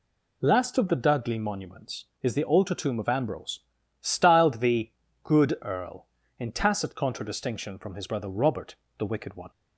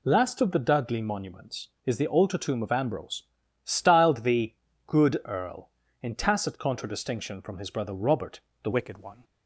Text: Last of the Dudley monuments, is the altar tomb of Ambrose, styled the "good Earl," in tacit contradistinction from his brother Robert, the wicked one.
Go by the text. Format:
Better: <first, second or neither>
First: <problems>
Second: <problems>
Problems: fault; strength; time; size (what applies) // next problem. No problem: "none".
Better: first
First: pauses between "the" and "good"; slight; at 4.9 s; 0.32 s long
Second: pauses between "the" and "good"; slight; at 4.5 s; 0.32 s long // changes voice at "wicked"; from 8.7 s on; 0.5 s long